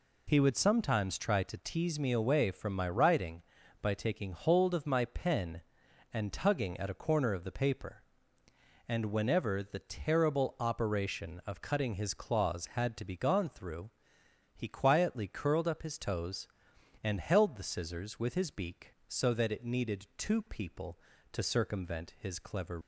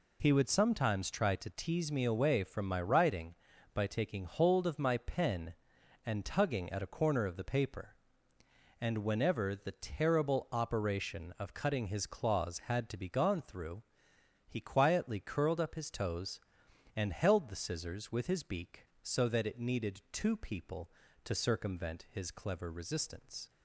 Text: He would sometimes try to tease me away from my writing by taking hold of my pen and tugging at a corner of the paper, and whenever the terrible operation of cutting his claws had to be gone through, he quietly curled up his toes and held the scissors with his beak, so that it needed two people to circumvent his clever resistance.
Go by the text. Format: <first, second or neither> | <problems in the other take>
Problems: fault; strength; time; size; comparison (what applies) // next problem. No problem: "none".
second | stops before "resistance"; at 22.8 s